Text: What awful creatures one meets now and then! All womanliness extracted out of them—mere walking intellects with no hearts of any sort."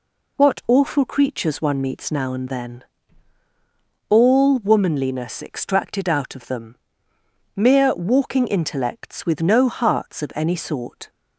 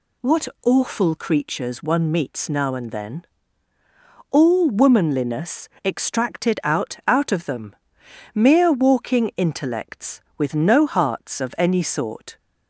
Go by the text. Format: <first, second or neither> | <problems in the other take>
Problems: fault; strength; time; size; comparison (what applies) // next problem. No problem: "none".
first | pauses between "What" and "awful"; slight; at 0.4 s; 0.18 s long // pauses between "womanliness" and "extracted"; slight; at 5.6 s; 0.16 s long // says "out" twice; at 7.0 s